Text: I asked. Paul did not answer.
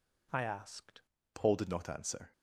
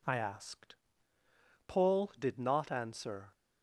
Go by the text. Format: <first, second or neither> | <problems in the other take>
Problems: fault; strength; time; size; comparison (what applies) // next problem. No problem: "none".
second | changes voice at "Paul"; from 1.3 s on; 1.0 s long